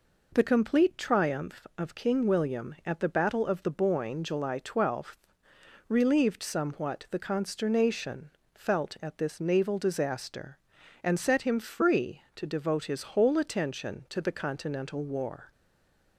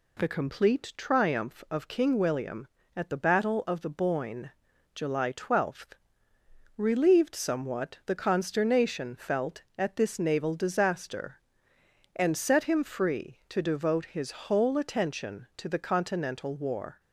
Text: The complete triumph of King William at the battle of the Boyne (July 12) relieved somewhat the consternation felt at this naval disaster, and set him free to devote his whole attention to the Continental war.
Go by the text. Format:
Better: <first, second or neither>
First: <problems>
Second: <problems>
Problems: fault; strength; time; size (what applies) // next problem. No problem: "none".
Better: second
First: pauses between "consternation" and "felt"; slight; at 8.3 s; 0.24 s long // stays silent after the last word; slight; from 15.5 s on; 0.6 s long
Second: none